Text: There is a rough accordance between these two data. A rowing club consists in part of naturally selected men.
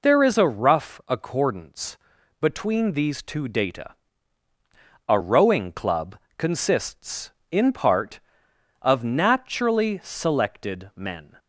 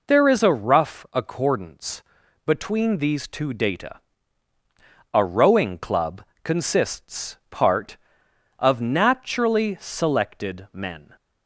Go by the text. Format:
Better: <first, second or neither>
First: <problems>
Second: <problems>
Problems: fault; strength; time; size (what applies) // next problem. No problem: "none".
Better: first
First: pauses between "accordance" and "between"; at 1.9 s; 0.44 s long // pauses between "club" and "consists"; slight; at 6.1 s; 0.20 s long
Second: pauses between "accordance" and "between"; at 2.0 s; 0.44 s long // pauses between "club" and "consists"; slight; at 6.2 s; 0.20 s long // skips "in"; at 7.4 s